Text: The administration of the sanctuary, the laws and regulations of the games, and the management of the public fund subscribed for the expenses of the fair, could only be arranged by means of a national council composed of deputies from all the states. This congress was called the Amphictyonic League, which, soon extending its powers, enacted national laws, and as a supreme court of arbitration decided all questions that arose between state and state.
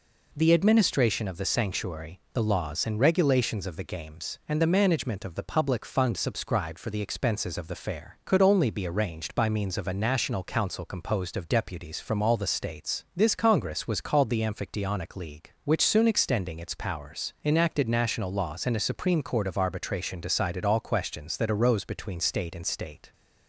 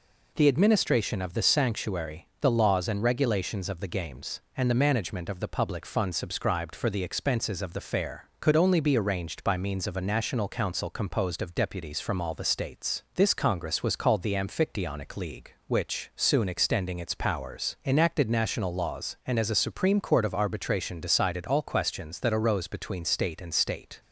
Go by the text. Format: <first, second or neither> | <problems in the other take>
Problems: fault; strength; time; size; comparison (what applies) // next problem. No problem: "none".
second | skips "as"; at 18.7 s